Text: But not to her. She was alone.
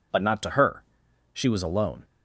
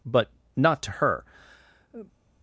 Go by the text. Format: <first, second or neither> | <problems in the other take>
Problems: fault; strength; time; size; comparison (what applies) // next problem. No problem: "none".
first | pauses between "But" and "not"; slight; at 0.3 s; 0.26 s long // stops before "She was alone"; at 2.0 s